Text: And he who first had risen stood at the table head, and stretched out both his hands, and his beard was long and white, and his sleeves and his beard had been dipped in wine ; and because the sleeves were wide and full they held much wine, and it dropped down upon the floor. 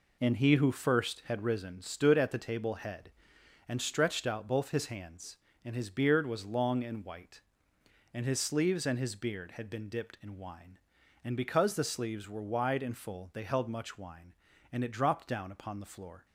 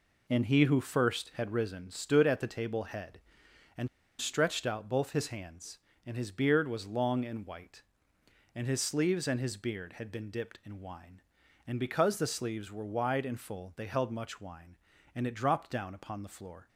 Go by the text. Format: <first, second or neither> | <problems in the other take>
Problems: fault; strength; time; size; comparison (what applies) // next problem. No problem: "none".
first | pauses between "and" and "stretched"; slight; at 3.8 s; 0.33 s long